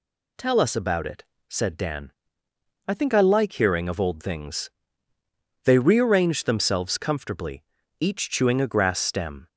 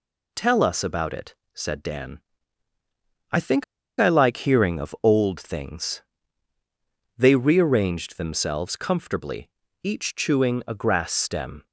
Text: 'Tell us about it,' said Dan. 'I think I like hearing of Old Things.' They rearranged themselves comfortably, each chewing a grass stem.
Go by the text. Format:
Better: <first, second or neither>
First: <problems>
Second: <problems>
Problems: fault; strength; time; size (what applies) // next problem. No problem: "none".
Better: first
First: none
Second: pauses between "think" and "I"; slight; at 3.6 s; 0.35 s long